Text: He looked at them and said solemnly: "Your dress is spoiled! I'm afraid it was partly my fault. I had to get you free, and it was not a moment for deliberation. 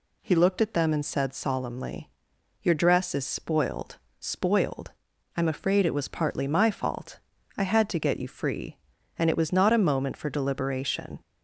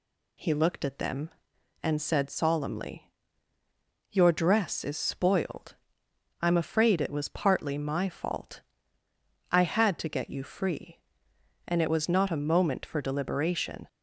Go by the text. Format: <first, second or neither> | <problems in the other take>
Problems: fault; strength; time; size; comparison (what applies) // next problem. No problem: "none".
second | says "spoiled" twice; at 4.1 s